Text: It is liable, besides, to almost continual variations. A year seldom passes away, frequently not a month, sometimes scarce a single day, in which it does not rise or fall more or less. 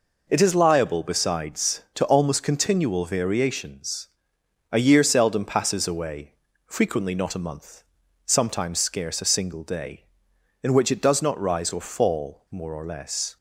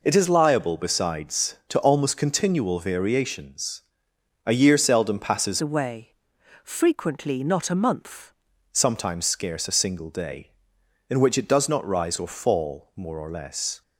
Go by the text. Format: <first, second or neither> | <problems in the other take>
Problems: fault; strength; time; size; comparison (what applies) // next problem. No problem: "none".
first | changes voice from "away" to "month"; from 5.6 to 8.3 s; 2.7 s long